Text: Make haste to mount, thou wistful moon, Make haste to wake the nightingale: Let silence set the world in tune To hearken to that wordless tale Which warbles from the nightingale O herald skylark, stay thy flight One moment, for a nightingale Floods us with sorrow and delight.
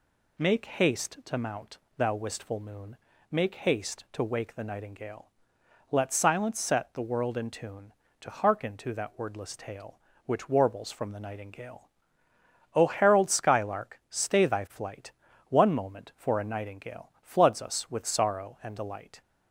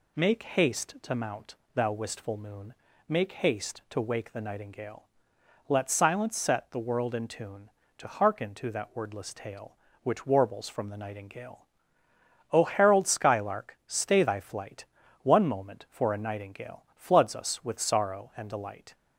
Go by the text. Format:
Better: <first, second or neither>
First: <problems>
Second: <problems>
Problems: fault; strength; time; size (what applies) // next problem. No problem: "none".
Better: neither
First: pauses between "nightingale" and "O"; noticeable; at 11.9 s; 0.84 s long // pauses between "flight" and "One"; at 15.1 s; 0.38 s long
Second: pauses between "nightingale" and "O"; noticeable; at 11.6 s; 0.84 s long // pauses between "flight" and "One"; at 14.8 s; 0.38 s long